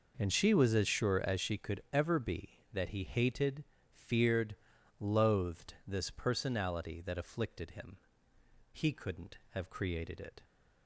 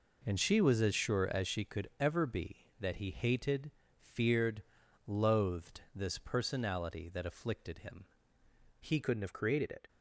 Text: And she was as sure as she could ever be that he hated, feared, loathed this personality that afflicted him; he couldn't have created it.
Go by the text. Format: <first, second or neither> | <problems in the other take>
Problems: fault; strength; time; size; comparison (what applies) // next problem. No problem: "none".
first | changes voice at "couldn't"; from 9.0 s on; 0.8 s long